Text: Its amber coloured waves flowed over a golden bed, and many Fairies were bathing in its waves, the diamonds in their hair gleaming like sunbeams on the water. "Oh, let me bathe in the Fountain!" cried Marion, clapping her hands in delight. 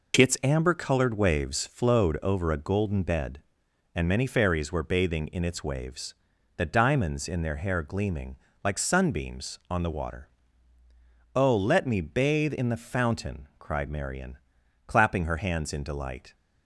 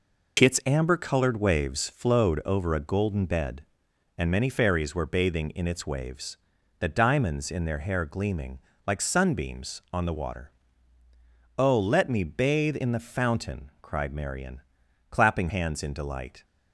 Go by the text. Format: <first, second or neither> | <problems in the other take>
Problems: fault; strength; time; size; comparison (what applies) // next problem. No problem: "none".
first | pauses between "gleaming" and "like"; slight; at 8.6 s; 0.26 s long; slight in the first // skips "her"; at 15.4 s